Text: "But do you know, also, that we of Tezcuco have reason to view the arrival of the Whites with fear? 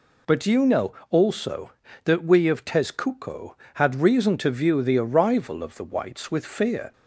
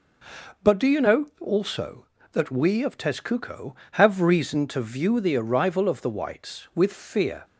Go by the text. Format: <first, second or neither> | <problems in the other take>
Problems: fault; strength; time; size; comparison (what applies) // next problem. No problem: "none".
second | says "had" for "have"; at 3.7 s